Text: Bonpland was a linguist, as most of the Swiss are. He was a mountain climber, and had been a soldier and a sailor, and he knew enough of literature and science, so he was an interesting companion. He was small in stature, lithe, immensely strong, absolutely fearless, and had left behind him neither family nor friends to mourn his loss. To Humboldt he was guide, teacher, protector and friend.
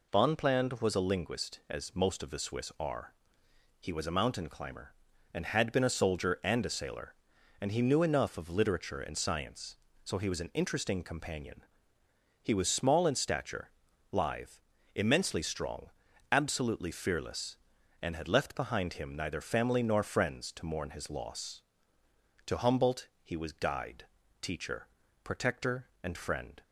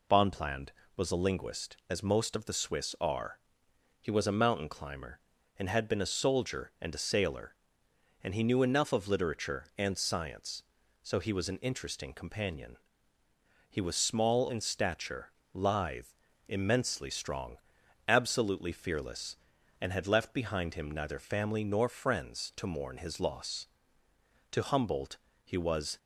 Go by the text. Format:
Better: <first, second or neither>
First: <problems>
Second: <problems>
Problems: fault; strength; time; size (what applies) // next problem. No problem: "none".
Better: first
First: none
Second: pauses between "Humboldt" and "he"; slight; at 25.1 s; 0.26 s long // stops before "guide teacher protector and friend"; at 25.9 s